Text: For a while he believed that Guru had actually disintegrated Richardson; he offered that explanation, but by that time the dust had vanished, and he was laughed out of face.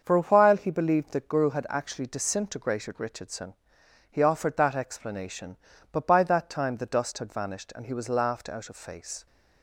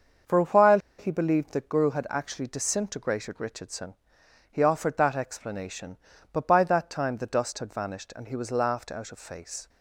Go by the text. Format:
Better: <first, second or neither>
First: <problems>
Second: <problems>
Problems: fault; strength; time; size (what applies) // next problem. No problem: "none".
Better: first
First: starts louder than the rest; until 1.0 s; 6.5 dB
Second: starts louder than the rest; until 1.4 s; 6.5 dB // pauses between "while" and "he"; slight; at 0.7 s; 0.19 s long